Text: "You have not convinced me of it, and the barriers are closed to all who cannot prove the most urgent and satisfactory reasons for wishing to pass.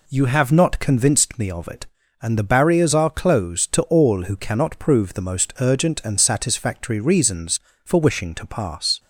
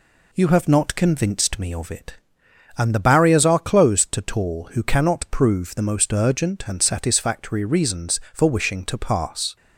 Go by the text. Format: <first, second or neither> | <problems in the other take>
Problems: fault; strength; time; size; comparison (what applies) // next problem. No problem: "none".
first | says "tall" for "all"; at 4.2 s